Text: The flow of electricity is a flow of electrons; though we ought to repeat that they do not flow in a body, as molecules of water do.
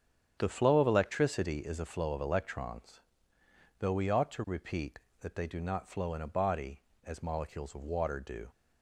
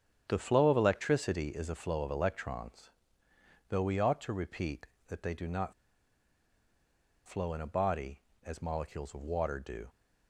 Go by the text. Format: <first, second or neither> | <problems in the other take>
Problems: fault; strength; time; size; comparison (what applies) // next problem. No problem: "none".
first | starts louder than the rest; strong; until 1.2 s; 8 dB; strong in the first // pauses between "not" and "flow"; strong; at 5.7 s; 1.5 s long